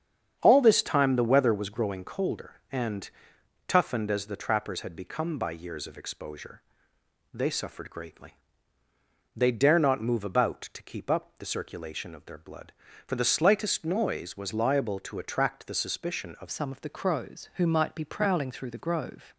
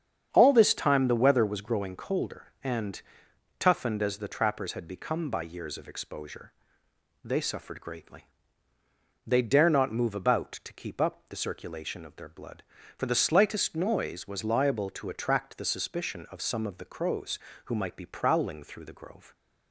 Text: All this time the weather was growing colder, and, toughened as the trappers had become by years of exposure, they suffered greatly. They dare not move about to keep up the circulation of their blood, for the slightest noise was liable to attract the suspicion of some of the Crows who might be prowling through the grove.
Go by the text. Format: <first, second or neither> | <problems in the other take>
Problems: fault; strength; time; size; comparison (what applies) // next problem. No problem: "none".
second | starts louder than the rest; strong; until 1.4 s; 8 dB; strong in the second // changes voice at "some"; from 16.5 s on; 2.8 s long